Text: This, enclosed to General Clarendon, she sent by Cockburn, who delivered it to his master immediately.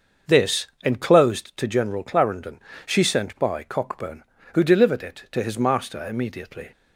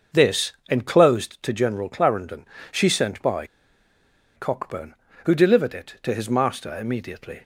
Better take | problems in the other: first | starts louder than the rest; noticeable; until 1.3 s; 6 dB; noticeable in the first // pauses between "by" and "Cockburn"; noticeable; at 3.4 s; 0.90 s long

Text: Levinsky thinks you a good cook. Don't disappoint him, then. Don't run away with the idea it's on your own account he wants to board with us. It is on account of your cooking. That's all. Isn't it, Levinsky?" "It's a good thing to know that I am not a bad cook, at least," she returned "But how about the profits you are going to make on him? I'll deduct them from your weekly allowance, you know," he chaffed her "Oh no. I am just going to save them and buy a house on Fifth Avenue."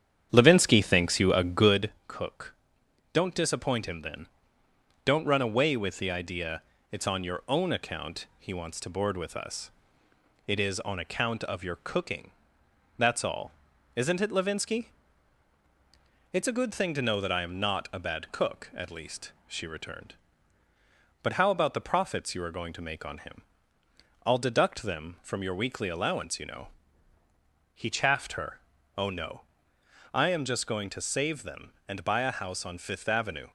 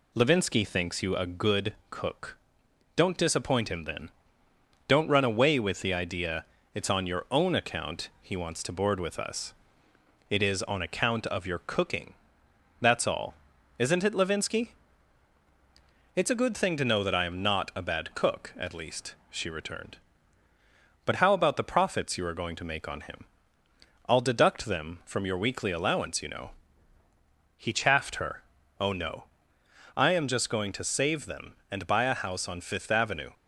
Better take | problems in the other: second | starts louder than the rest; strong; until 1.9 s; 9 dB // pauses between "good" and "cook"; slight; at 1.8 s; 0.16 s long; slight in the second // pauses between "idea" and "it's"; slight; at 6.6 s; 0.30 s long; slight in the second // pauses between "her" and "Oh"; slight; at 28.5 s; 0.36 s long; slight in the second

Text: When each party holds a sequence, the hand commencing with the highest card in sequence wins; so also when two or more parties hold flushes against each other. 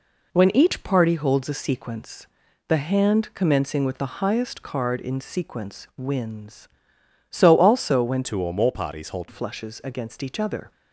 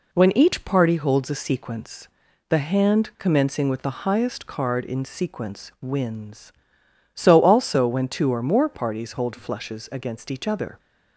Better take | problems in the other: second | changes voice from "two" to "hold"; from 8.2 to 9.2 s; 1.0 s long

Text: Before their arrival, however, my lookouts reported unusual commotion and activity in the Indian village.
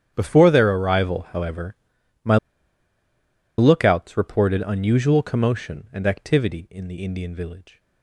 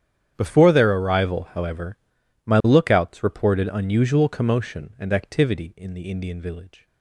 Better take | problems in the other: second | starts louder than the rest; strong; until 1.1 s; 9 dB; strong in the second // pauses between "my" and "lookouts"; at 2.3 s; 1.2 s long

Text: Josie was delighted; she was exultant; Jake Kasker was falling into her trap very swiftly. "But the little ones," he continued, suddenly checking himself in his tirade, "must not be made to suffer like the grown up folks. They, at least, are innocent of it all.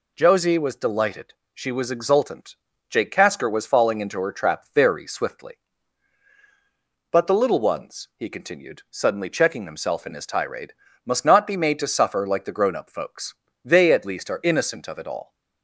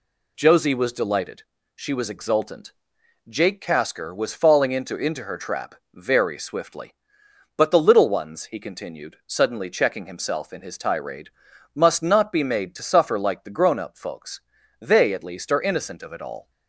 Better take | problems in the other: first | says "into" twice; at 4.9 s // pauses between "trap" and "very"; slight; at 5.7 s; 0.18 s long

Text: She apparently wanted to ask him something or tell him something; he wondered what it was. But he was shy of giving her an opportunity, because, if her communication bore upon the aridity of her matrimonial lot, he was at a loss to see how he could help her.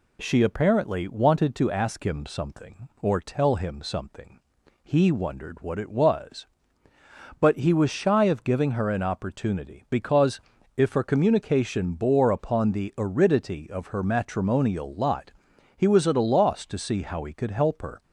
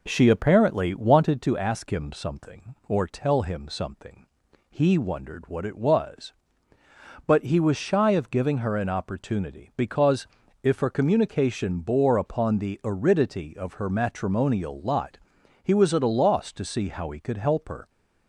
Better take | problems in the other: first | starts louder than the rest; noticeable; until 1.3 s; 4 dB

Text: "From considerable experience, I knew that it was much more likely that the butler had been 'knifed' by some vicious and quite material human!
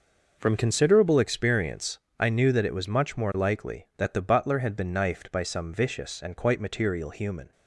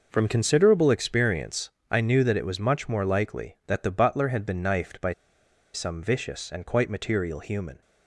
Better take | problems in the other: first | pauses between "by" and "some"; noticeable; at 5.1 s; 0.61 s long

